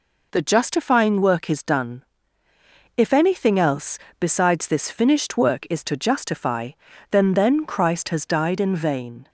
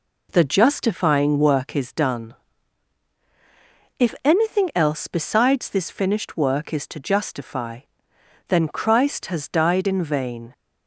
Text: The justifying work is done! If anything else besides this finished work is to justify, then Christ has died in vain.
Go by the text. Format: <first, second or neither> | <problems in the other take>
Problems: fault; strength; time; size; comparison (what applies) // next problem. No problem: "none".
second | pauses between "else" and "besides"; slight; at 3.9 s; 0.24 s long // says "then" twice; at 7.3 s